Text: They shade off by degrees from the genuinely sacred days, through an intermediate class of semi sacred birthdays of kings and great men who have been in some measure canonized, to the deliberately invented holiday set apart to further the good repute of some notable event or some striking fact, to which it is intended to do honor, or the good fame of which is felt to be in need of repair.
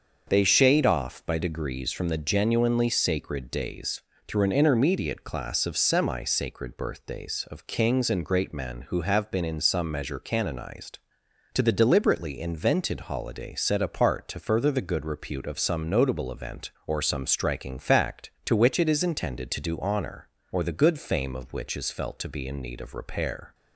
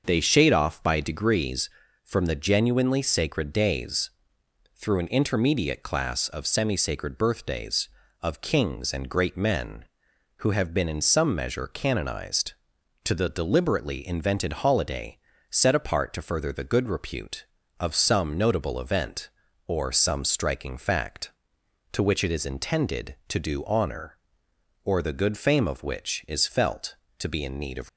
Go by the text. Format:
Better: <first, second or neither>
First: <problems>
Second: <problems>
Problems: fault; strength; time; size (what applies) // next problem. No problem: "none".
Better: first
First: starts louder than the rest; until 1.2 s; 6 dB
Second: starts louder than the rest; until 1.0 s; 6.5 dB // pauses between "holiday" and "set"; slight; at 15.1 s; 0.32 s long // stops before "repair"; at 27.8 s